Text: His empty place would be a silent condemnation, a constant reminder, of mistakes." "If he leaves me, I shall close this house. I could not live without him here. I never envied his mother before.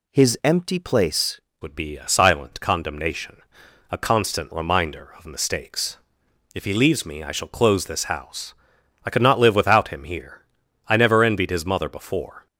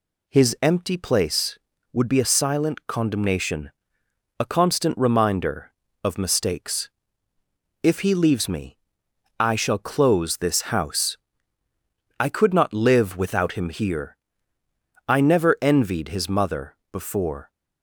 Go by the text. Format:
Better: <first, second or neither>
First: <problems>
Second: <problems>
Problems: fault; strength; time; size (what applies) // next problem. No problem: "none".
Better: second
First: changes voice at "would"; from 1.6 s on; 10.8 s long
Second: none